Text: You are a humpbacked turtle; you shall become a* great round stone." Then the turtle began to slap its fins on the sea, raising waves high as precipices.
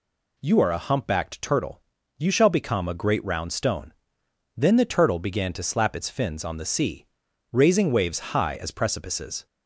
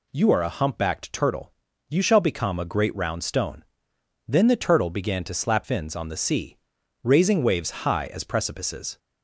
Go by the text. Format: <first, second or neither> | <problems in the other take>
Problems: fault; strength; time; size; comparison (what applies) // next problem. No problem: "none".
first | skips "its"; at 5.6 s